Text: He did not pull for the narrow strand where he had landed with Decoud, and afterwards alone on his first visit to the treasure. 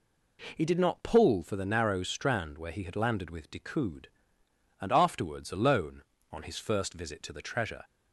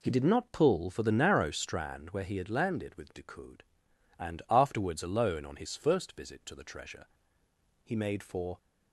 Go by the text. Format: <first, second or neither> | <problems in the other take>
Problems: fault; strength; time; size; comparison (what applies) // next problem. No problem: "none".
first | goes on to say "He made for"; noticeable; from 7.8 s on; 0.74 s long